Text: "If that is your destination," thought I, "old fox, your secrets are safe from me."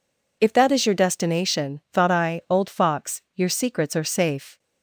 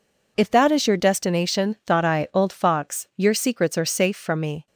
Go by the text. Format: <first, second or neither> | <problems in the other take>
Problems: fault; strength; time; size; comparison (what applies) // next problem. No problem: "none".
second | stops before "from me"; at 4.5 s